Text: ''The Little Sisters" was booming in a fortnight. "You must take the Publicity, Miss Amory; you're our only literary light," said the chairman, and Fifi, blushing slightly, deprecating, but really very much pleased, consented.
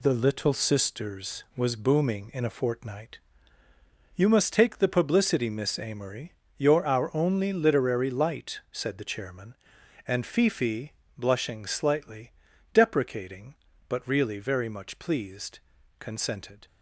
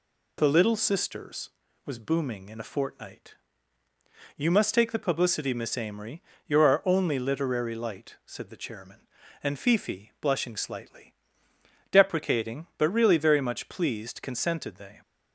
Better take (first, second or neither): first